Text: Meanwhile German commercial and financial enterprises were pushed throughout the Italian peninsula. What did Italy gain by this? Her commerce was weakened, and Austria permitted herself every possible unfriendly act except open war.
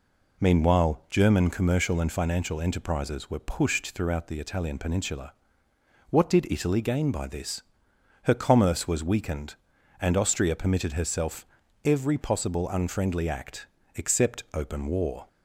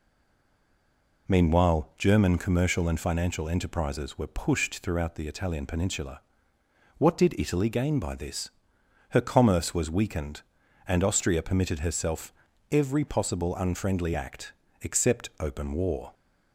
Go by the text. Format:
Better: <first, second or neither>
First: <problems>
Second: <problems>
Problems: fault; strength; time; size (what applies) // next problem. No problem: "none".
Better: first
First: pauses between "herself" and "every"; at 11.4 s; 0.38 s long // pauses between "act" and "except"; slight; at 13.6 s; 0.30 s long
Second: stays silent before the first word; noticeable; until 1.2 s; 1.2 s long // pauses between "herself" and "every"; at 12.3 s; 0.38 s long // pauses between "act" and "except"; slight; at 14.5 s; 0.30 s long